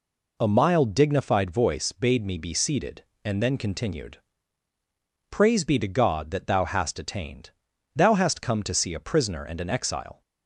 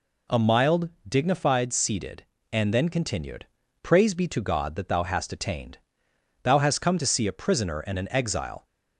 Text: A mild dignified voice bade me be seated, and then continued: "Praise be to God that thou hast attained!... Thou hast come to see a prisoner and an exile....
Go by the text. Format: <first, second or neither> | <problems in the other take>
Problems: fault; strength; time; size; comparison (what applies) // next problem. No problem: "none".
first | pauses between "mild" and "dignified"; slight; at 0.8 s; 0.18 s long // skips "voice bade me be"; at 1.7 s